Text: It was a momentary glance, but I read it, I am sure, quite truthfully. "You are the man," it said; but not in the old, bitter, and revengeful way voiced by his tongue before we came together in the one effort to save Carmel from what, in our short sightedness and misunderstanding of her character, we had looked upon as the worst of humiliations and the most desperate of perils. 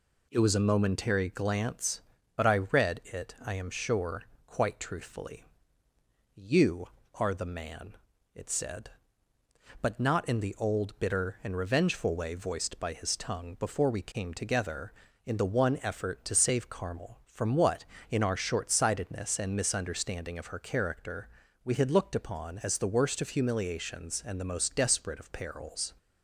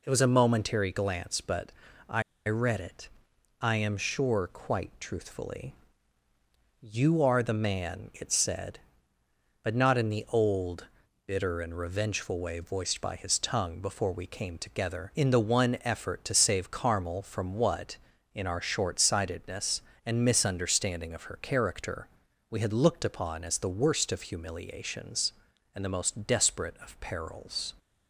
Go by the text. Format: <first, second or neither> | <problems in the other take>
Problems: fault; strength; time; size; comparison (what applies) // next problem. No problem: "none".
first | pauses between "but" and "I"; slight; at 1.7 s; 0.36 s long // pauses between "I" and "read"; slight; at 2.2 s; 0.25 s long